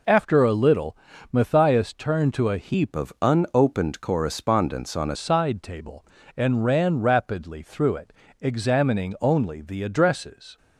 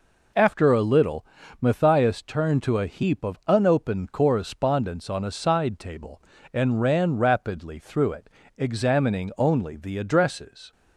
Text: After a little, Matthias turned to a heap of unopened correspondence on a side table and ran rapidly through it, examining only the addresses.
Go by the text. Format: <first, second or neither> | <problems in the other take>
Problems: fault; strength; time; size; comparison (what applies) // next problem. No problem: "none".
second | changes voice from "of" to "a"; from 2.9 to 5.1 s; 2.2 s long